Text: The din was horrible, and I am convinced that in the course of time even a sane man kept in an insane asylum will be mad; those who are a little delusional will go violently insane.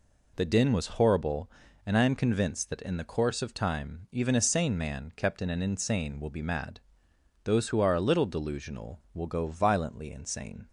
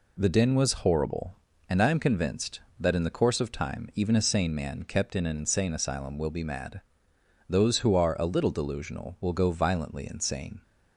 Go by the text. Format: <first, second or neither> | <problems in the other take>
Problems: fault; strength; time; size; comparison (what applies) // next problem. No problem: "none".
second | skips "asylum"; at 6.1 s